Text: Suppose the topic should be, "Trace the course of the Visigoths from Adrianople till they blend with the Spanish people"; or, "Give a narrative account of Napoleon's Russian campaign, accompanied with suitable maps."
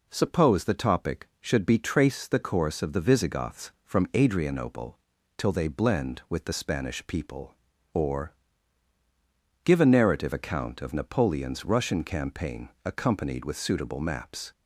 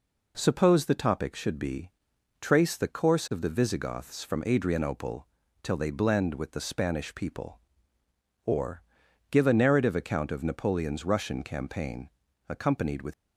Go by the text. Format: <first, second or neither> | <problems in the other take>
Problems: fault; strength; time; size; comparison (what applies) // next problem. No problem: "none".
first | pauses between "Adrianople" and "till"; slight; at 5.2 s; 0.36 s long; also in the first // stops before "suitable maps"; at 13.1 s